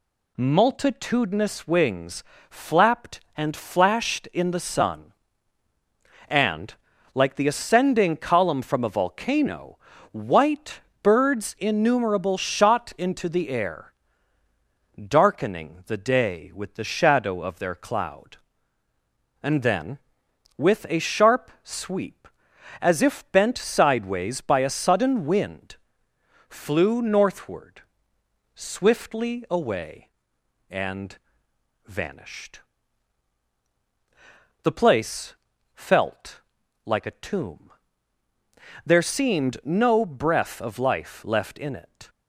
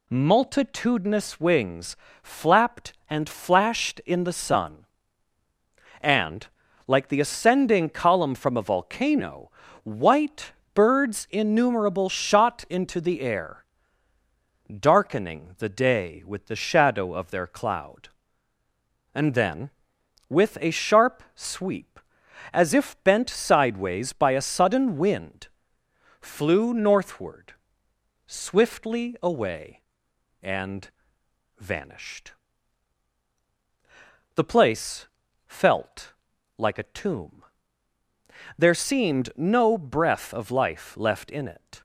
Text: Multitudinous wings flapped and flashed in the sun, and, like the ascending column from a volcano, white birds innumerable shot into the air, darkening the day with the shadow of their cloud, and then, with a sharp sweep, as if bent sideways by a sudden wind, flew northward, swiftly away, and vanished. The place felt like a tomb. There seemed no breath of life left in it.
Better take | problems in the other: neither | pauses between "wings" and "flapped"; slight; the same in both // pauses between "white" and "birds"; slight; the same in both // pauses between "and" and "vanished"; noticeable; the same in both // pauses between "place" and "felt"; the same in both // pauses between "felt" and "like"; the same in both

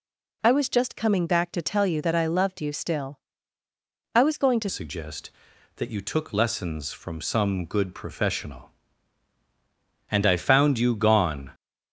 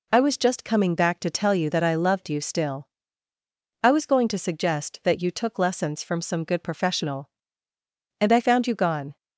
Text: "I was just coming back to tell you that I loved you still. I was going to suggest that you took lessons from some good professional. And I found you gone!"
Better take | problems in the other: second | changes voice at "suggest"; from 4.6 s on; 6.9 s long

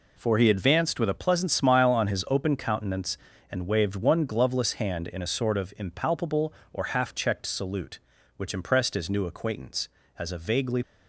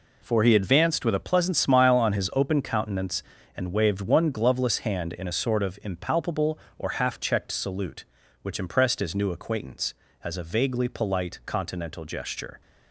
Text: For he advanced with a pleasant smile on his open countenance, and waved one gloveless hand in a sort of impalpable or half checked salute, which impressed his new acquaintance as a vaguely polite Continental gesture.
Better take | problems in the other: second | stops before "polite Continental gesture"; at 10.8 s

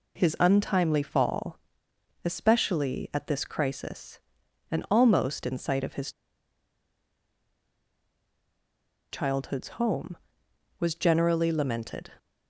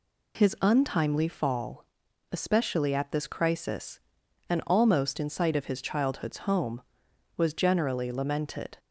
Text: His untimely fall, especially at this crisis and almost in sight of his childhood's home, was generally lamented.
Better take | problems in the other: second | pauses between "his" and "childhood's"; strong; at 6.1 s; 3.0 s long

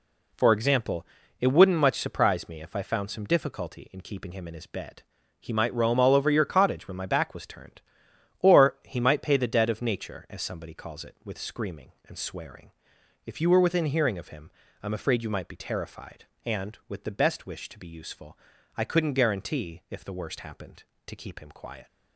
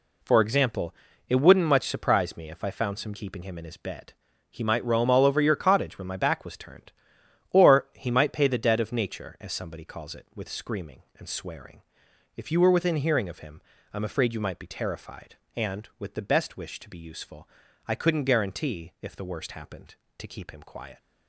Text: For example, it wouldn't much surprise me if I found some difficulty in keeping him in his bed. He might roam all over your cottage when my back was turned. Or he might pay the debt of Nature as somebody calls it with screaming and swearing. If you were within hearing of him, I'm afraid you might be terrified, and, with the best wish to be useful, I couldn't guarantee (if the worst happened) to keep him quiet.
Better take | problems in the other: first | skips "difficulty in"; at 3.1 s

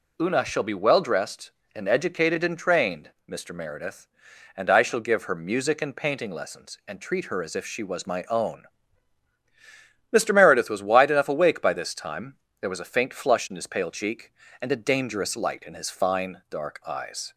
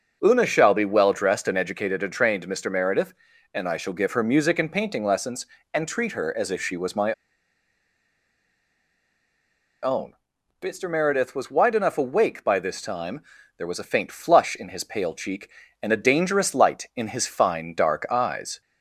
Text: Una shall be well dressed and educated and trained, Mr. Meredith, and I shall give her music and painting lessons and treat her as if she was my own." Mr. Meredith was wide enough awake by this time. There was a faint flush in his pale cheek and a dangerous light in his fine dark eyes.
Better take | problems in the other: first | starts louder than the rest; noticeable; until 1.2 s; 6 dB // pauses between "my" and "own"; strong; at 7.1 s; 2.7 s long

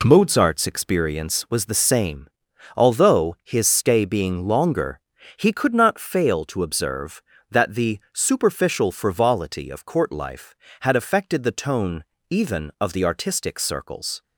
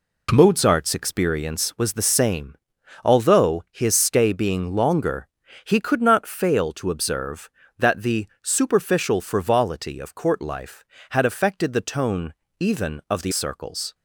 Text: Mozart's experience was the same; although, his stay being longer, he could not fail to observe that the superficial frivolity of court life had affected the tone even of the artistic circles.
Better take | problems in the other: first | pauses between "the" and "superficial"; slight; at 8.2 s; 0.16 s long // pauses between "tone" and "even"; slight; at 12.3 s; 0.26 s long; slight in the first // skips "artistic"; at 13.3 s

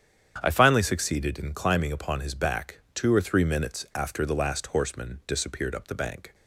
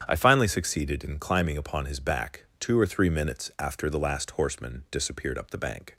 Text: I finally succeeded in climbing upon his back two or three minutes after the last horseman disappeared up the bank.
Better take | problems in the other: neither | starts louder than the rest; strong; the same in both

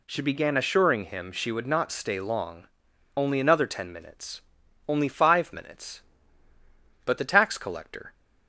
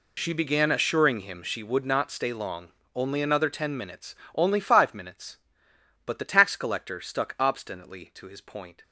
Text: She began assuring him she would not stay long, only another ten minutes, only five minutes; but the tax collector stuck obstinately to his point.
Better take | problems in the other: second | stops before "stuck obstinately to his point"; at 8.1 s

